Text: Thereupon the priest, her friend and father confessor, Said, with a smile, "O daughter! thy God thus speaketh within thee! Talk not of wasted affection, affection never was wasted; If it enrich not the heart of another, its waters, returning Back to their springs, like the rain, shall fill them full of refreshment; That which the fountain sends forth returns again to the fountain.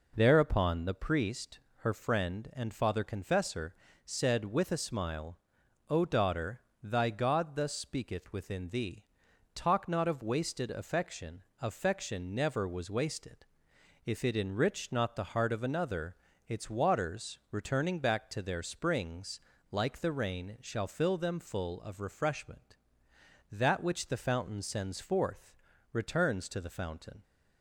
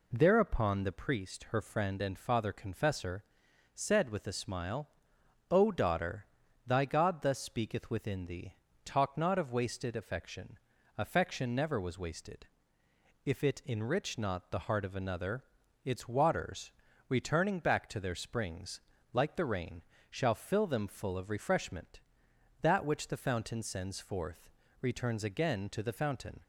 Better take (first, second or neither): second